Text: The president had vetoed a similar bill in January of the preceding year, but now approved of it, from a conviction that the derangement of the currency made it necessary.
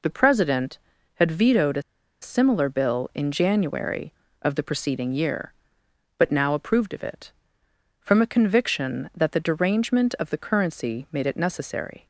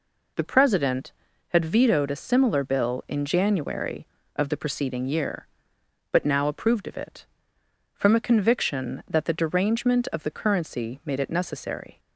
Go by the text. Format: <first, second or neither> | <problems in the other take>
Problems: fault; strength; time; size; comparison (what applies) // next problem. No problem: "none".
second | pauses between "a" and "similar"; at 1.8 s; 0.39 s long